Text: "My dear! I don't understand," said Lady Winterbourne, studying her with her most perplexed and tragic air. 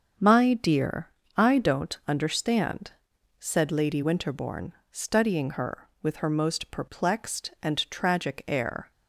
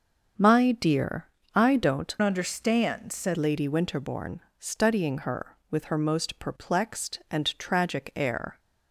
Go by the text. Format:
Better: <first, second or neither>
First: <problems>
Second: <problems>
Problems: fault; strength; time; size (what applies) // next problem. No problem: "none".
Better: first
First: starts louder than the rest; until 1.4 s; 7 dB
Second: starts louder than the rest; until 1.6 s; 7 dB // changes voice from "understand" to "said"; from 2.2 to 3.3 s; 1.1 s long